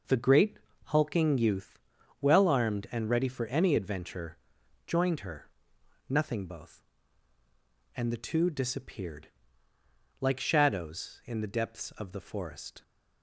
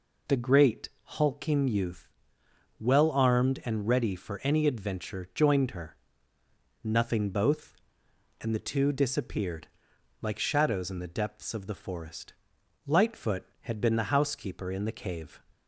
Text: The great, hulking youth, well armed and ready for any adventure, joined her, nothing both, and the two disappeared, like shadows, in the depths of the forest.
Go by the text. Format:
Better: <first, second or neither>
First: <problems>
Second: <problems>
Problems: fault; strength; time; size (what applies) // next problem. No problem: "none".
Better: first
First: none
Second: goes on to say "Lightfoot had been the housekeeper in the cave"; strong; from 12.8 s on; 2.5 s long